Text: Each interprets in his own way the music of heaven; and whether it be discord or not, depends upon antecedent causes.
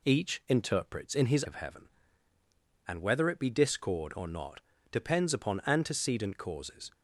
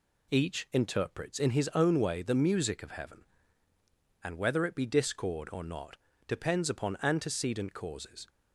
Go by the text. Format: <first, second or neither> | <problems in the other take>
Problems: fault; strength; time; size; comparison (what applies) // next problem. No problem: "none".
second | skips "own way the music"; at 1.4 s